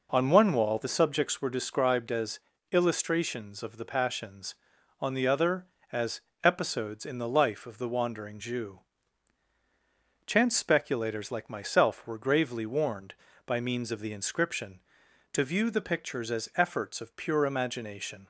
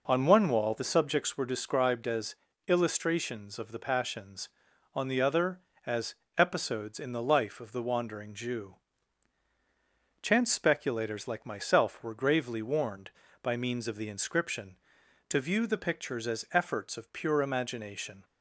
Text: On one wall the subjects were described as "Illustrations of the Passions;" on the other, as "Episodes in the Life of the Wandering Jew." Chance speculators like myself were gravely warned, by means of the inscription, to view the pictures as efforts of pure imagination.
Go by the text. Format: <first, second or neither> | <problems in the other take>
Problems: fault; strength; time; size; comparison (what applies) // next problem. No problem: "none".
neither | pauses between "as" and "Illustrations"; slight; the same in both // pauses between "as" and "Episodes"; slight; the same in both